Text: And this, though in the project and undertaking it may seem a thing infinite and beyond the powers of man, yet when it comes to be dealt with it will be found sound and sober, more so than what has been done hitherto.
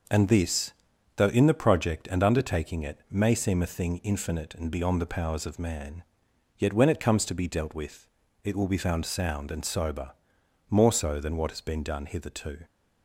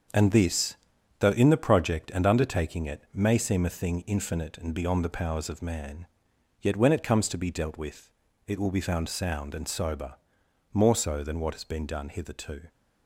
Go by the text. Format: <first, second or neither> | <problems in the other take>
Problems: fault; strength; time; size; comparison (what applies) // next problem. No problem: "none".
first | gets quieter; strong; throughout; 7.5 dB // pauses between "with" and "it"; slight; at 8.1 s; 0.36 s long; slight in the first